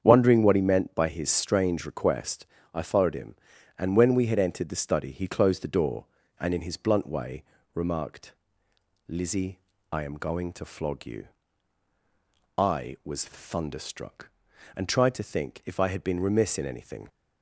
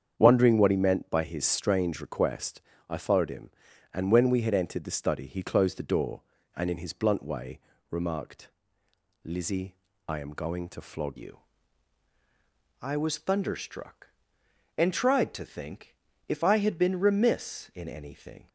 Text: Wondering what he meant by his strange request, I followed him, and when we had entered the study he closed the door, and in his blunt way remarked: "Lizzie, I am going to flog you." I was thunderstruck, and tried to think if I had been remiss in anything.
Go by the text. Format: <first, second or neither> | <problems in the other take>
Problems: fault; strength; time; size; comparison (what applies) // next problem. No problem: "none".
first | starts louder than the rest; strong; until 1.1 s; 7.5 dB; strong in the first // pauses between "way" and "remarked"; slight; at 7.5 s; 0.32 s long; slight in the first // changes voice at "you"; from 11.1 s on; 7.3 s long // pauses between "think" and "if"; slight; at 15.9 s; 0.32 s long